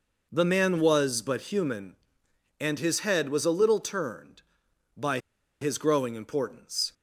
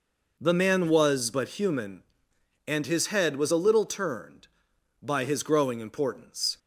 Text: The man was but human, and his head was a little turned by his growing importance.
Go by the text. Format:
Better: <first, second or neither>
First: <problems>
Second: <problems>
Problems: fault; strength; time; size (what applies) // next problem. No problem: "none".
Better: second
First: pauses between "by" and "his"; at 5.1 s; 0.42 s long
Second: none